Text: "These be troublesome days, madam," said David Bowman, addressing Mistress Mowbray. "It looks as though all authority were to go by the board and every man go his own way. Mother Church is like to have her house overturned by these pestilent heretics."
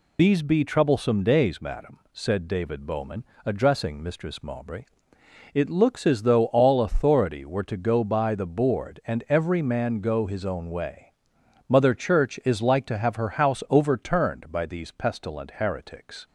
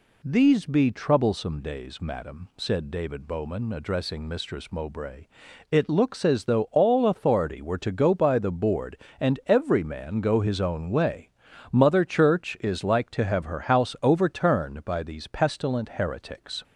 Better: second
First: loses the start of "These"; at 0.1 s; 55 ms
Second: none

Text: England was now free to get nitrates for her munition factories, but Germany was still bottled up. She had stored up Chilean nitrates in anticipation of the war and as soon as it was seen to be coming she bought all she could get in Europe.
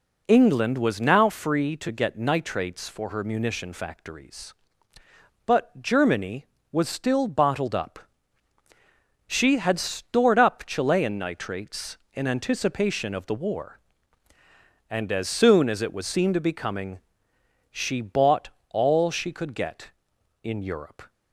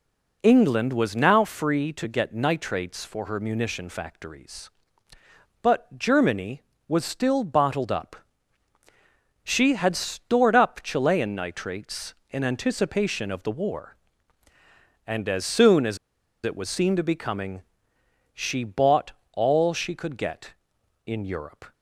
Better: first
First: pauses between "coming" and "she"; noticeable; at 16.9 s; 0.72 s long // pauses between "bought" and "all"; slight; at 18.4 s; 0.22 s long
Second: pauses between "as" and "it"; noticeable; at 15.9 s; 0.48 s long // pauses between "coming" and "she"; noticeable; at 17.6 s; 0.72 s long // pauses between "bought" and "all"; slight; at 19.1 s; 0.22 s long

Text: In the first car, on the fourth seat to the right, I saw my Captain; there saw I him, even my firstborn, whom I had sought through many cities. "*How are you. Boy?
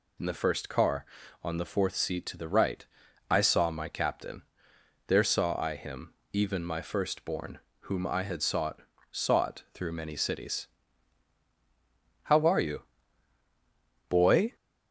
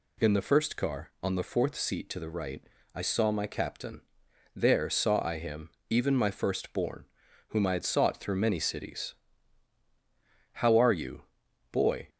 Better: second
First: says "sought" twice; at 9.0 s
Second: none

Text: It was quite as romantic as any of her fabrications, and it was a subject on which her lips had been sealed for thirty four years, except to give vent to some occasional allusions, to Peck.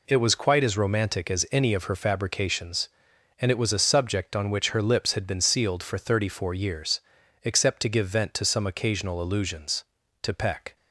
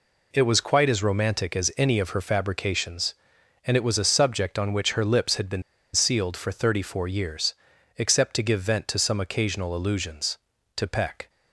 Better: first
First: none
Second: pauses between "been" and "sealed"; slight; at 5.6 s; 0.32 s long

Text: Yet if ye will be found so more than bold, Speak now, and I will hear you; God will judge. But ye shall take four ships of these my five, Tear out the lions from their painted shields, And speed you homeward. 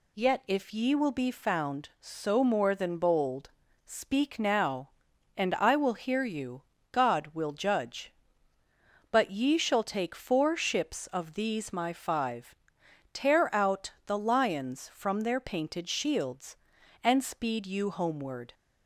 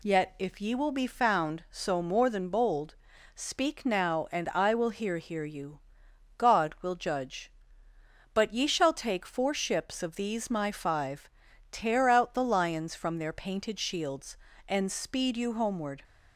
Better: first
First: none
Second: says "hear" twice; at 5.1 s

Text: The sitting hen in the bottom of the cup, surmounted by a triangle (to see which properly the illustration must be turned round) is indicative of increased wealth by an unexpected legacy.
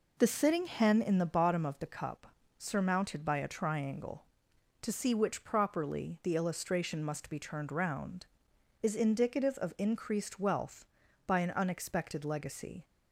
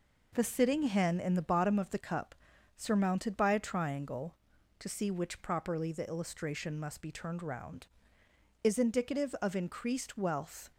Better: first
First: none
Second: stops before "by an unexpected legacy"; at 10.7 s

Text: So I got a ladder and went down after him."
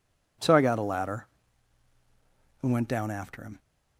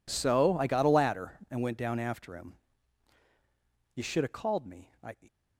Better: first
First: none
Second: goes on to say "You should have called me I"; noticeable; from 3.9 s on; 1.2 s long

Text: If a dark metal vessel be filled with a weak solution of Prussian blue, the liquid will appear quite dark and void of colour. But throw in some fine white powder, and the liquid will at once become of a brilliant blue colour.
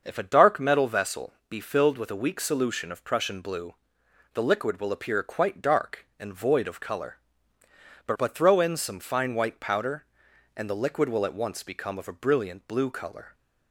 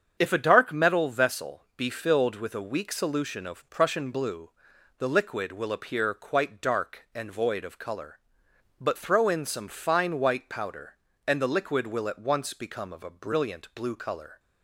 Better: second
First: starts louder than the rest; until 1.0 s; 6.5 dB // pauses between "vessel" and "be"; slight; at 1.3 s; 0.16 s long // says "But" twice; at 8.1 s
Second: starts louder than the rest; strong; until 1.2 s; 7.5 dB // pauses between "vessel" and "be"; slight; at 1.6 s; 0.16 s long

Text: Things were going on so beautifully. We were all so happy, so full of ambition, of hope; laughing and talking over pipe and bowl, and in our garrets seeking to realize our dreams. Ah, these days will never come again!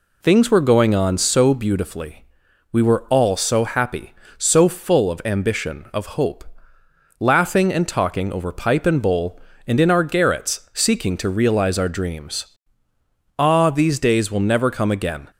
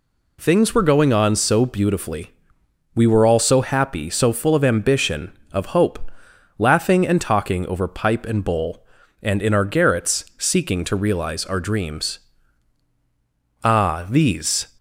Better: first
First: none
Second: stops before "days will never come again"; at 14.7 s

